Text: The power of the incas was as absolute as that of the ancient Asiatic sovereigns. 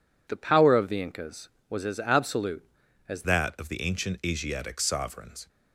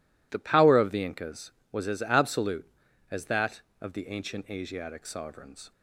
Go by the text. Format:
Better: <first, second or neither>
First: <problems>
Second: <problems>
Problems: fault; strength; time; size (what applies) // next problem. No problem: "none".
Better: second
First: changes voice at "that"; from 3.2 s on; 2.2 s long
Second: none